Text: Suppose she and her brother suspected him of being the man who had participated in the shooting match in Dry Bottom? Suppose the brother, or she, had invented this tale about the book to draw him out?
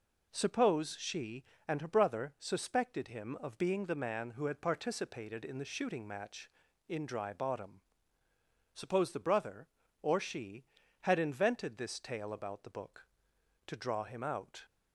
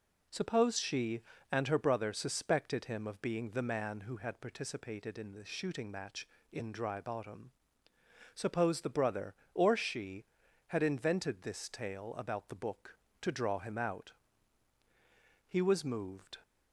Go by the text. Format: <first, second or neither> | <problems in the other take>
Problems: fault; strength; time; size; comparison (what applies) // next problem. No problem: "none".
first | goes on to say "He was moved"; noticeable; from 15.4 s on; 0.90 s long